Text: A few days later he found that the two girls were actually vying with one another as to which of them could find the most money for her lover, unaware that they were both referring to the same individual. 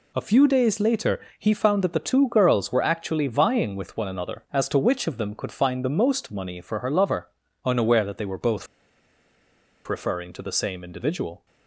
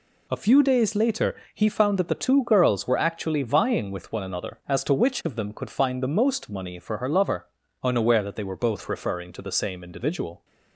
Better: second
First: pauses between "later" and "he"; slight; at 1.2 s; 0.18 s long // pauses between "both" and "referring"; at 8.6 s; 1.2 s long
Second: pauses between "later" and "he"; slight; at 1.3 s; 0.18 s long

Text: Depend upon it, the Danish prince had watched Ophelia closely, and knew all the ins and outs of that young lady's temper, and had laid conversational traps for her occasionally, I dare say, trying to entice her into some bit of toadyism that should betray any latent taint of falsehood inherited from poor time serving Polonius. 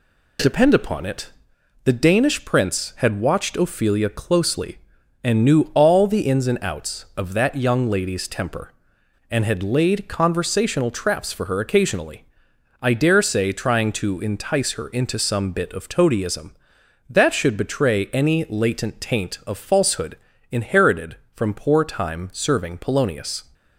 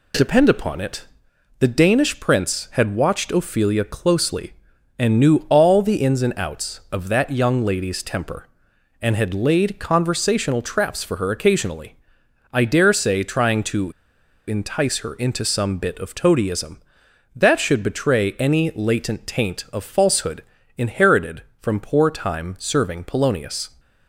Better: first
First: pauses between "falsehood" and "inherited"; slight; at 20.1 s; 0.36 s long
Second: pauses between "to" and "entice"; noticeable; at 13.9 s; 0.55 s long // pauses between "falsehood" and "inherited"; slight; at 20.4 s; 0.36 s long

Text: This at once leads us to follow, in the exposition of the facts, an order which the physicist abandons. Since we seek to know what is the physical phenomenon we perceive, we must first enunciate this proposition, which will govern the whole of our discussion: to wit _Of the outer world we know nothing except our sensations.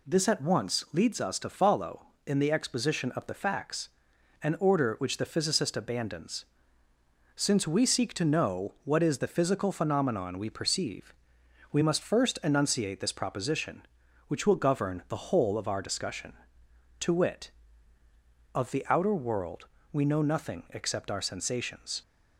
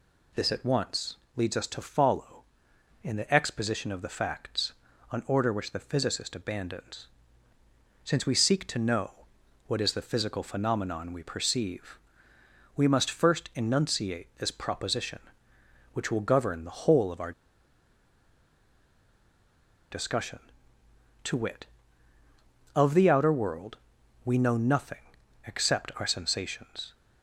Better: first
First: pauses between "world" and "we"; slight; at 19.6 s; 0.24 s long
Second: pauses between "once" and "leads"; slight; at 1.1 s; 0.20 s long // pauses between "know" and "what"; noticeable; at 9.1 s; 0.56 s long // pauses between "our" and "discussion"; strong; at 17.3 s; 2.6 s long // pauses between "world" and "we"; noticeable; at 23.7 s; 0.46 s long // pauses between "nothing" and "except"; at 25.0 s; 0.40 s long

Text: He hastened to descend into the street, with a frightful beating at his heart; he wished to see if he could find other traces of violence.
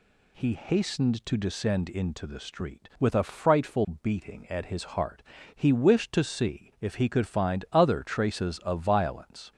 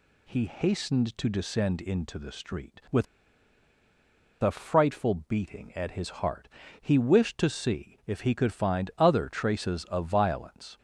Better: first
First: none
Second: pauses between "with" and "a"; strong; at 3.0 s; 1.3 s long

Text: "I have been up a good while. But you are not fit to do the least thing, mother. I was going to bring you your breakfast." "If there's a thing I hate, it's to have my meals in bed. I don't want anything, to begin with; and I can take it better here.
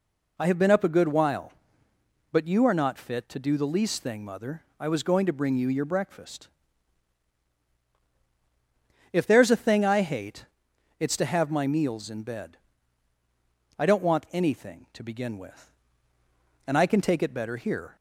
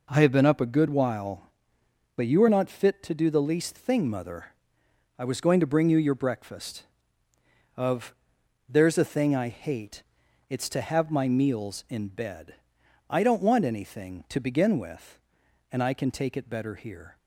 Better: first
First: none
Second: says "Of" for "If"; at 7.7 s

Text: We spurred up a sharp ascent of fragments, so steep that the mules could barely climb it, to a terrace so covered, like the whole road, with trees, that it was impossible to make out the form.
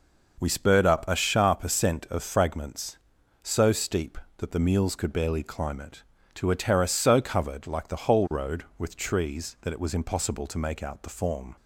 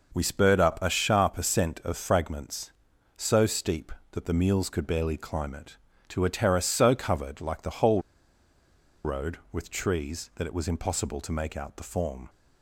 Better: first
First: none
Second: pauses between "whole" and "road"; at 8.0 s; 1.0 s long

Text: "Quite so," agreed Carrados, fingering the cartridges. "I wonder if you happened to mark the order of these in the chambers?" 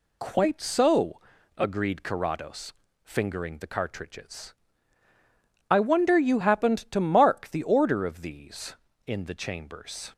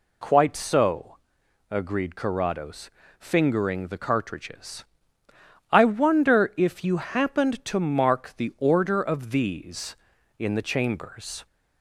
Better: second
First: skips "if"; at 6.1 s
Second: none

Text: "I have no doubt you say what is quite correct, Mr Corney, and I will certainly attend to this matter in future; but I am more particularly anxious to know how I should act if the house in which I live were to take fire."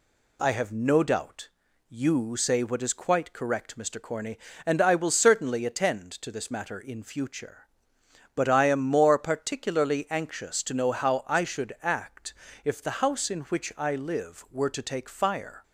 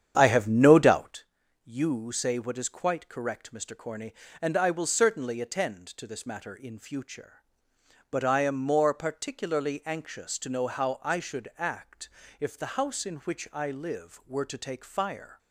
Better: first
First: pauses between "doubt" and "you"; at 1.4 s; 0.42 s long // pauses between "act" and "if"; slight; at 12.3 s; 0.32 s long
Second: starts louder than the rest; strong; until 1.2 s; 9 dB // pauses between "doubt" and "you"; at 1.2 s; 0.42 s long // pauses between "act" and "if"; slight; at 12.0 s; 0.32 s long

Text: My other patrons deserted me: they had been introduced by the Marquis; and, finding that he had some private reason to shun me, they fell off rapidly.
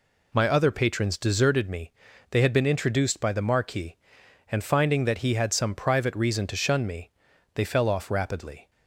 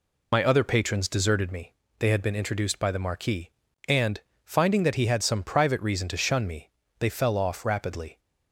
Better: first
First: none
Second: loses the start of "My"; at 0.3 s; 50 ms

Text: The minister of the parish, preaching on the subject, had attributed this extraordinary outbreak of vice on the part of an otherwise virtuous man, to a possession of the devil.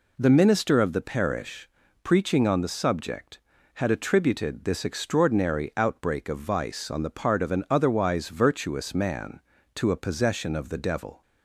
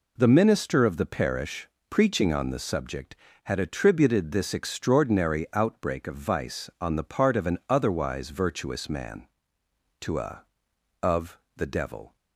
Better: first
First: none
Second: skips "possession"; at 10.7 s // pauses between "of" and "the"; slight; at 11.3 s; 0.20 s long

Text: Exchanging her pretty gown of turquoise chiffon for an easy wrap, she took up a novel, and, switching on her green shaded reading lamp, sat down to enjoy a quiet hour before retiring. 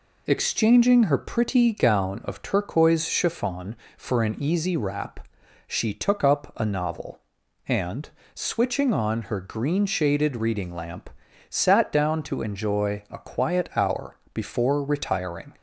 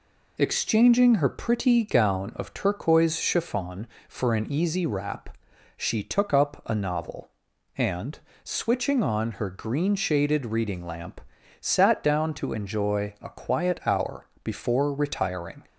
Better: neither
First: pauses between "hour" and "before"; slight; at 14.1 s; 0.16 s long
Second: pauses between "hour" and "before"; slight; at 14.2 s; 0.16 s long

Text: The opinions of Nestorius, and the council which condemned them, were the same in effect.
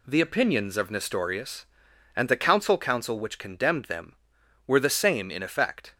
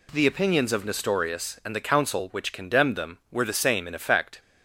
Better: second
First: says "council" twice; at 2.7 s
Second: none

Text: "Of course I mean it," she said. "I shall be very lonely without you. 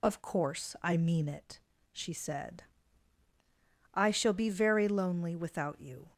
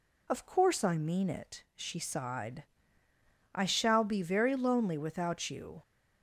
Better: first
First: none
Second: says "sighed" for "said"; at 1.9 s

